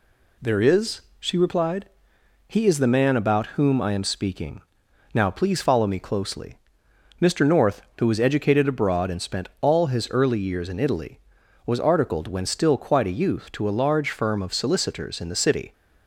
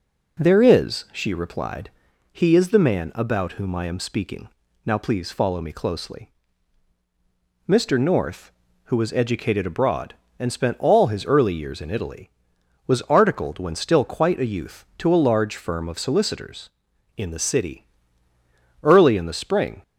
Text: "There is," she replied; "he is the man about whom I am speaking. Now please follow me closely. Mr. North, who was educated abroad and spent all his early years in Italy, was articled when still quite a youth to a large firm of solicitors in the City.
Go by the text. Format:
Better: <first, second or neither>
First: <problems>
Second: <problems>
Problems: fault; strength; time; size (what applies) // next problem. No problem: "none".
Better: first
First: none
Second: goes on to say "Early in the spring"; noticeable; from 18.8 s on; 0.98 s long